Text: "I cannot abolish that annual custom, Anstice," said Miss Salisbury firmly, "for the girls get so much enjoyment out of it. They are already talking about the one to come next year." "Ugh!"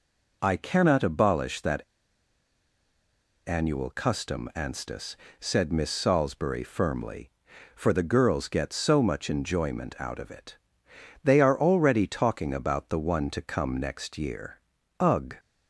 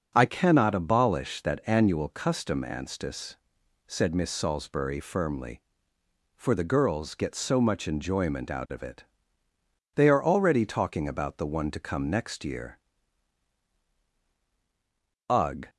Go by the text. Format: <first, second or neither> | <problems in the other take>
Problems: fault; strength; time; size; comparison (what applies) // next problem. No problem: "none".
second | pauses between "that" and "annual"; strong; at 1.8 s; 1.6 s long